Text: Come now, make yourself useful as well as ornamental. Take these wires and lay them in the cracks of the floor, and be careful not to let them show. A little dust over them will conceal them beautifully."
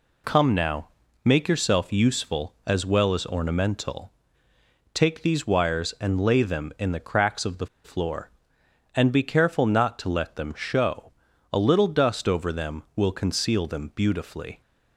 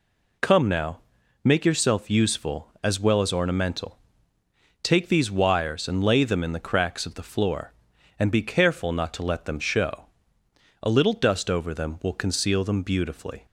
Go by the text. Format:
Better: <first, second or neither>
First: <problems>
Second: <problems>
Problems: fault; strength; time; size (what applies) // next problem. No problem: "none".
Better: second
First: pauses between "the" and "floor"; slight; at 7.6 s; 0.17 s long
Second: none